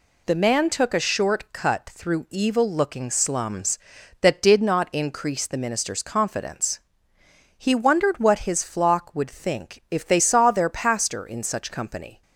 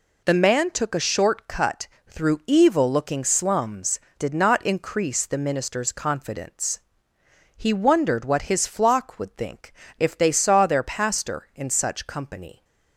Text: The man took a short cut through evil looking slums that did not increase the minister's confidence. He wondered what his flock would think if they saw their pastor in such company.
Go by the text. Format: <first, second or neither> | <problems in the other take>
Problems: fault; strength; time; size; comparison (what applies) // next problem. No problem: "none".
first | pauses between "cut" and "through"; slight; at 1.8 s; 0.20 s long // skips "that"; at 4.0 s // pauses between "think" and "if"; slight; at 9.7 s; 0.26 s long